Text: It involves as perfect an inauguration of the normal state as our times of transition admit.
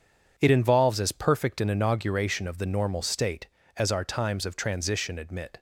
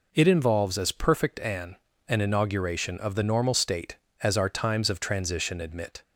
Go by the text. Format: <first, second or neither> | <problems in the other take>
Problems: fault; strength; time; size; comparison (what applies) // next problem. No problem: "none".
first | says "an" twice; at 2.0 s